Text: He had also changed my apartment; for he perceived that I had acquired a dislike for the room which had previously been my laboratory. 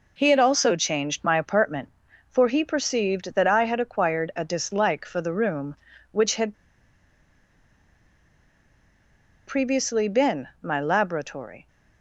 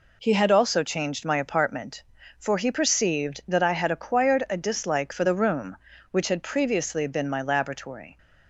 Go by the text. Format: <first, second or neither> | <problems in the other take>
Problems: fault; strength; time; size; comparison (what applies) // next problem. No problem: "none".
second | pauses between "had" and "previously"; strong; at 6.5 s; 2.9 s long